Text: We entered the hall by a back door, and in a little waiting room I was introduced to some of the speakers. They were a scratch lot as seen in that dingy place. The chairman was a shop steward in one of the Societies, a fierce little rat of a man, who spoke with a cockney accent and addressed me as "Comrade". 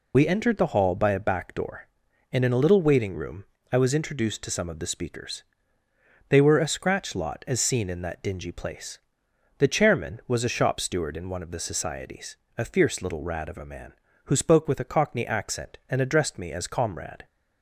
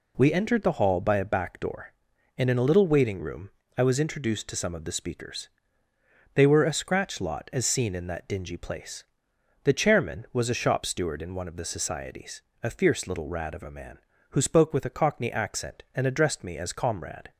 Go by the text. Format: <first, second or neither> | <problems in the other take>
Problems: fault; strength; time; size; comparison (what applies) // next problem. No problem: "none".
second | loses the start of "We"; at 0.1 s; 55 ms // pauses between "room" and "I"; slight; at 3.4 s; 0.26 s long; slight in the second